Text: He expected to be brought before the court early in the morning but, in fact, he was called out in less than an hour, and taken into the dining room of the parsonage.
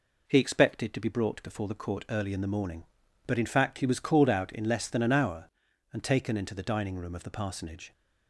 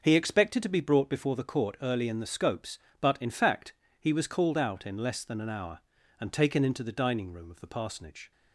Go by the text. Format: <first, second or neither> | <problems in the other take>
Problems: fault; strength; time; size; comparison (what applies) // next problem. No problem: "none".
first | says "scopes" for "morning"; at 2.2 s